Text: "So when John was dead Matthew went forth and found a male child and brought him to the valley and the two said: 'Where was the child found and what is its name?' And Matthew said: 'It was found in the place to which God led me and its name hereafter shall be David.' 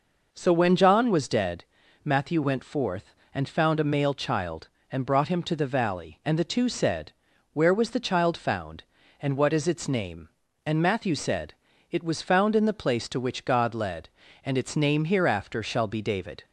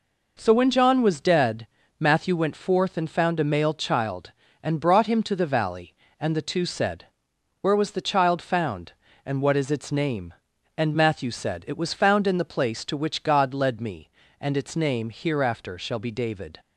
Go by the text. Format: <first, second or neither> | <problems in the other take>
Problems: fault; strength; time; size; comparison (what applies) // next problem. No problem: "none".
second | pauses between "dead" and "Matthew"; at 1.6 s; 0.40 s long; slight in the second // skips "me"; at 14.2 s